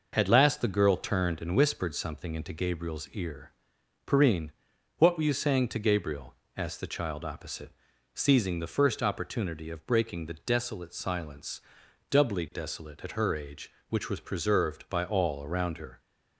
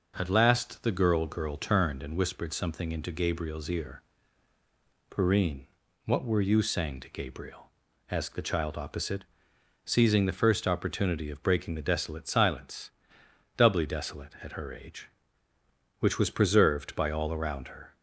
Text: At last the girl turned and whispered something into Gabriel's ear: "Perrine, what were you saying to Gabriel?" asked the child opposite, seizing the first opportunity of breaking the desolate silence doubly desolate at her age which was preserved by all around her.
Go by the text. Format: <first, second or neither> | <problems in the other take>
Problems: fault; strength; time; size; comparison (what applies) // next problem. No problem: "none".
first | says "girl" twice; at 1.2 s // pauses between "silence" and "doubly"; noticeable; at 12.9 s; 0.64 s long; noticeable in the first